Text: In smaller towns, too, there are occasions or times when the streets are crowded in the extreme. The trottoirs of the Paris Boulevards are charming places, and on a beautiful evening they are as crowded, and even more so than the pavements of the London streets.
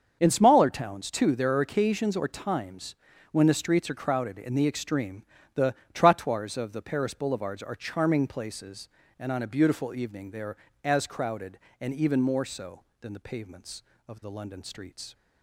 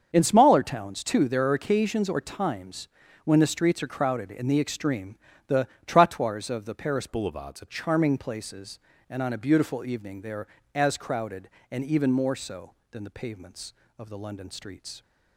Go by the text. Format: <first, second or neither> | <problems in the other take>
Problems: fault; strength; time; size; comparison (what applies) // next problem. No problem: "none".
first | starts louder than the rest; until 1.1 s; 6.5 dB; also in the first // pauses between "times" and "when"; at 2.8 s; 0.38 s long; also in the first // pauses between "The" and "trottoirs"; slight; at 5.6 s; 0.18 s long; slight in the first // changes voice from "Boulevards" to "are"; from 7.0 to 7.6 s; 0.6 s long